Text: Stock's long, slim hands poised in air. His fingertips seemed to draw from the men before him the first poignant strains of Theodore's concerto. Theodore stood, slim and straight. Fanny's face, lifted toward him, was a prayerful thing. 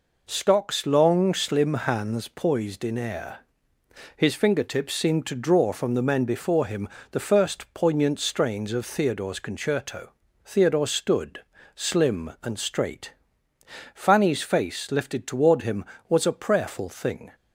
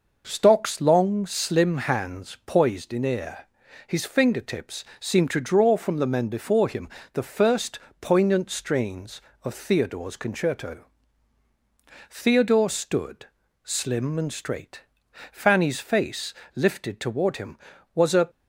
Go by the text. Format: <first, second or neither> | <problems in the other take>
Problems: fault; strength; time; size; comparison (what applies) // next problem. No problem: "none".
first | pauses between "him" and "the"; slight; at 6.8 s; 0.26 s long; slight in the first // pauses between "first" and "poignant"; slight; at 7.7 s; 0.22 s long // stops before "prayerful thing"; at 18.2 s